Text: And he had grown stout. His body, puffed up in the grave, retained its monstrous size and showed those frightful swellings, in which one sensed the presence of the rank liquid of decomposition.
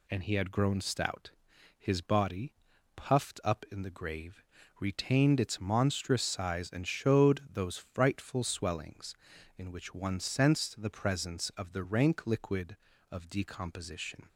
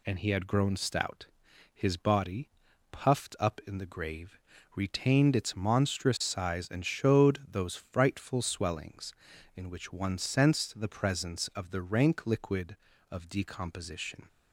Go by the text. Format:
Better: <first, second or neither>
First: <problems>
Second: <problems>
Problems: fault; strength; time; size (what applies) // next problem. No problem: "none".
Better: neither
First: none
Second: none